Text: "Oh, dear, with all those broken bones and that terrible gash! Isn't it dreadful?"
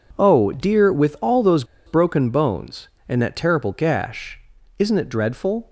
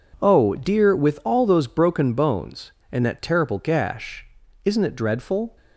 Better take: second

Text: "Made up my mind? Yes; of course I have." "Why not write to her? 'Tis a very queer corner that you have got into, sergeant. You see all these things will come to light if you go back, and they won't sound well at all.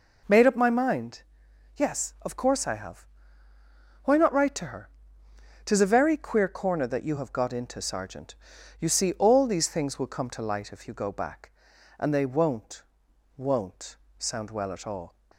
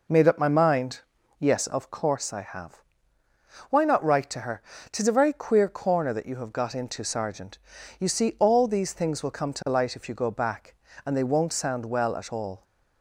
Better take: second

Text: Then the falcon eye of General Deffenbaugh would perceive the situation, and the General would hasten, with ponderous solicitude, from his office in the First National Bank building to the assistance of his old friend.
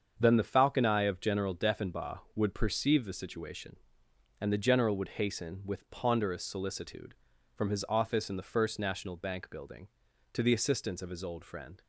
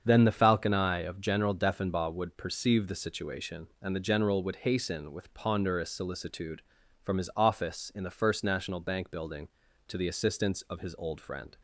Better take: neither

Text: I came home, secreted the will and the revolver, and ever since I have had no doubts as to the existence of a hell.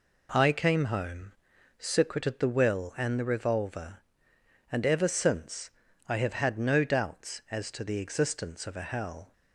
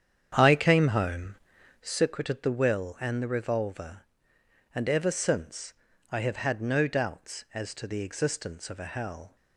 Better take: first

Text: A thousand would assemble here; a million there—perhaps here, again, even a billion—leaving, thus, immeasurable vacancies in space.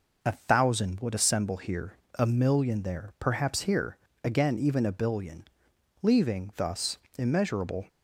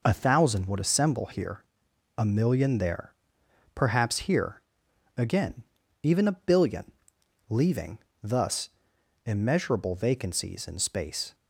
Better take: second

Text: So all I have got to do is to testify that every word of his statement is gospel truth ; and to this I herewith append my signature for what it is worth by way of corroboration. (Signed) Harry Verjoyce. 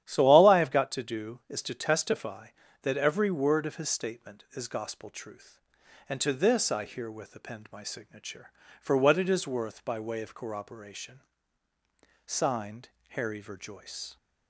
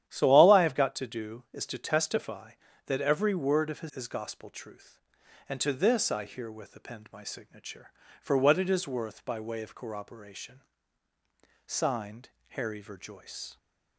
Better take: first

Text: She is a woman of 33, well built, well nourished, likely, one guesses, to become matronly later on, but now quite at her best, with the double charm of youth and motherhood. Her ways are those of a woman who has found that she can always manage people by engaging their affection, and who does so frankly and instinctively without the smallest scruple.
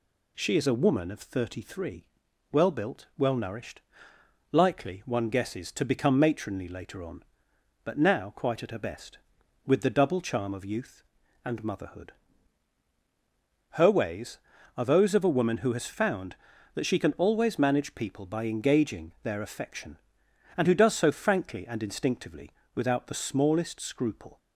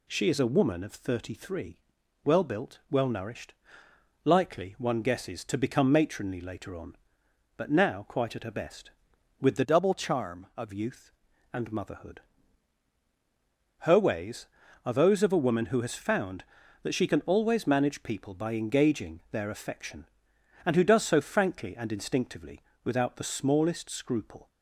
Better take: first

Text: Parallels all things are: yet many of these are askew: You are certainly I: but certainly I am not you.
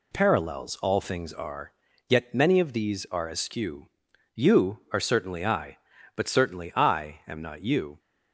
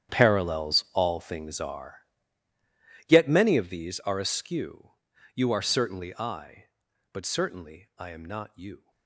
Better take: first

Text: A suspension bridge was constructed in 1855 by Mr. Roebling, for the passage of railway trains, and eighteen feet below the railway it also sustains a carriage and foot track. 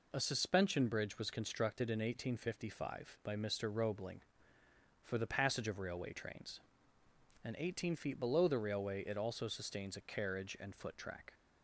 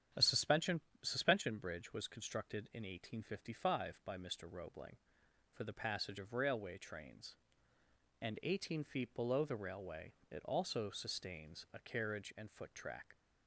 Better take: first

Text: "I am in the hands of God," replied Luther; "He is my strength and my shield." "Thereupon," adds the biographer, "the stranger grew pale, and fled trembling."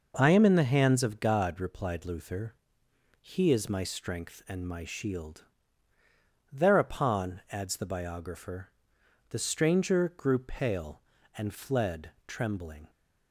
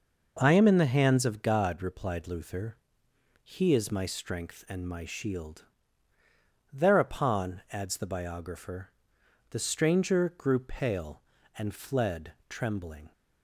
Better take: neither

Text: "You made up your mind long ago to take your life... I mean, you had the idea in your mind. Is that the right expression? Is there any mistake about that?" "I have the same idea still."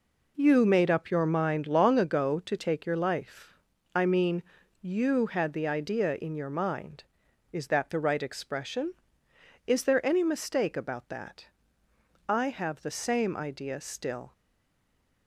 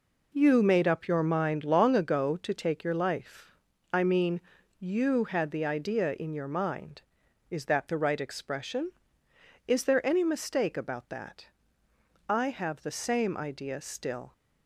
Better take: second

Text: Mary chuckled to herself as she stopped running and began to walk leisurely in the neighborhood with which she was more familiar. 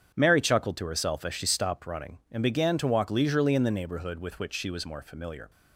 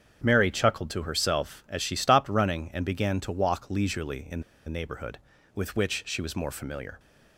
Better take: first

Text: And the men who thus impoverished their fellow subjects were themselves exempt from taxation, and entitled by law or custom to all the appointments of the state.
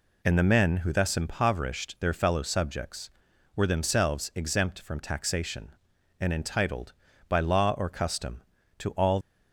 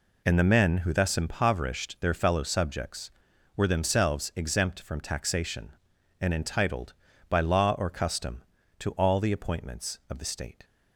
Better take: second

